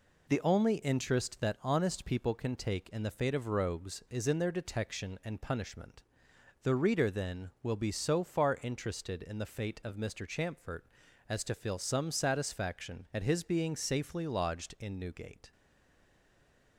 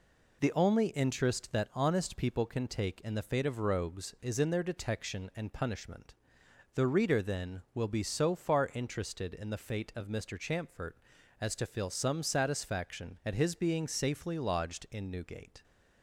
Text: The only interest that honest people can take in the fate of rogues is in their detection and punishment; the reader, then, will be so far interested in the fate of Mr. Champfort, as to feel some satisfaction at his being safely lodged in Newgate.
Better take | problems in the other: second | stays silent after the last word; noticeable; from 15.5 s on; 1.2 s long

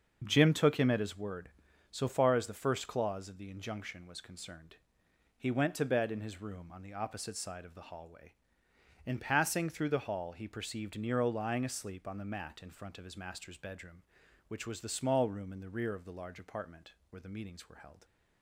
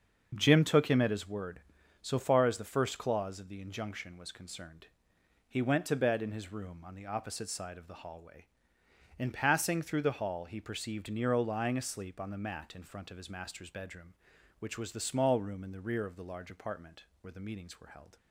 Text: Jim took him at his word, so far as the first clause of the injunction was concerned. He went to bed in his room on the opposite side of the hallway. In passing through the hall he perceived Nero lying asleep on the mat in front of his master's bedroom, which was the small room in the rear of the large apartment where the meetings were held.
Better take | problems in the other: neither | starts louder than the rest; the same in both // pauses between "apartment" and "where"; slight; the same in both

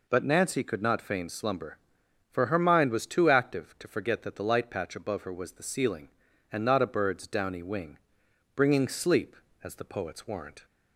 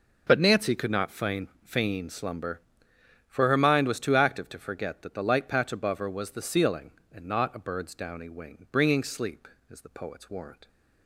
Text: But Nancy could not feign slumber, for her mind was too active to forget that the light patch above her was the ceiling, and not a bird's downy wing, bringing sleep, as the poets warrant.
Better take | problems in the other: first | says "feign" twice; at 1.6 s

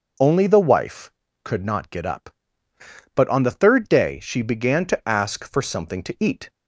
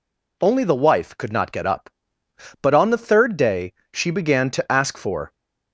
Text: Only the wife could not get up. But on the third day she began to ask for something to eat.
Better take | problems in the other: first | pauses between "day" and "she"; slight; at 3.7 s; 0.18 s long // stops before "something to eat"; at 5.3 s

